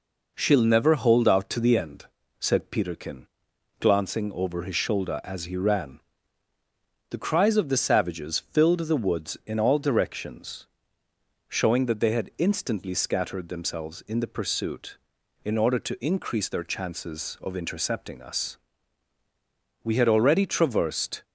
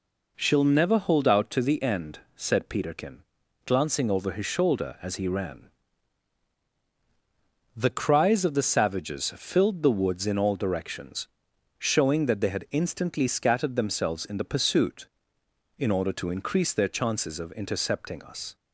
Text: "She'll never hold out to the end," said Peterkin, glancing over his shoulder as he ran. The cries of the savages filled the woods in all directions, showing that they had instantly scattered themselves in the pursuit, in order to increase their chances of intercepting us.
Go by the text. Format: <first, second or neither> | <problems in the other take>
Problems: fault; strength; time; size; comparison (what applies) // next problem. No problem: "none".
second | goes on to say "We had already traversed"; from 19.8 s on; 1.3 s long